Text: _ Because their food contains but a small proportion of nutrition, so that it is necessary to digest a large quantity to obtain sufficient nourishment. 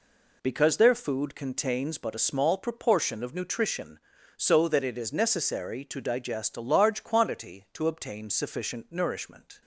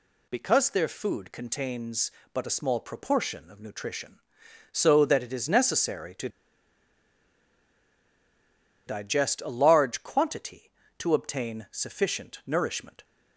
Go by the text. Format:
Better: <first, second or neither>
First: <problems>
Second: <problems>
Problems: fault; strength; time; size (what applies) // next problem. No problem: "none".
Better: first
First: none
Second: pauses between "to" and "digest"; strong; at 6.2 s; 2.5 s long